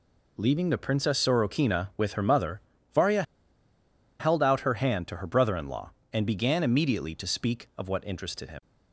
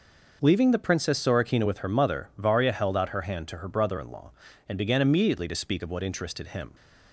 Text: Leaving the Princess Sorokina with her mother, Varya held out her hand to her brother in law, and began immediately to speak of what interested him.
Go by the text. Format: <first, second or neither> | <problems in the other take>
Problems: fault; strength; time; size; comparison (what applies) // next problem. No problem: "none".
second | pauses between "Varya" and "held"; noticeable; at 3.2 s; 0.97 s long